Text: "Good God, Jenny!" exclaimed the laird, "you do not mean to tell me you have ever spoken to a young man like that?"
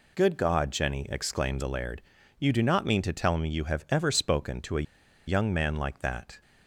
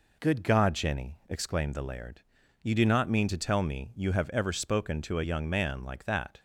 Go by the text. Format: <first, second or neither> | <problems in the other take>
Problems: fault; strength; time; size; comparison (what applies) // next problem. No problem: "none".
second | pauses between "a" and "young"; at 4.8 s; 0.43 s long